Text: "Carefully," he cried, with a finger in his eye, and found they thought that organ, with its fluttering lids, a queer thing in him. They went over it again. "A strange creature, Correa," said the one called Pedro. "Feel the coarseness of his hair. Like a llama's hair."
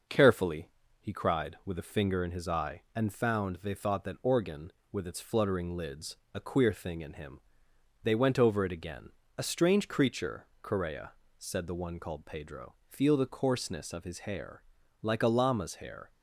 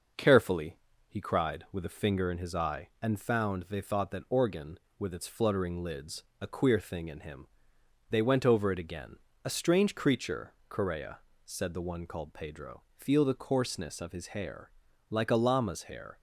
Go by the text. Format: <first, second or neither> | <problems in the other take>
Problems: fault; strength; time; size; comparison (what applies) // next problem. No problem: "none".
neither | starts louder than the rest; noticeable; the same in both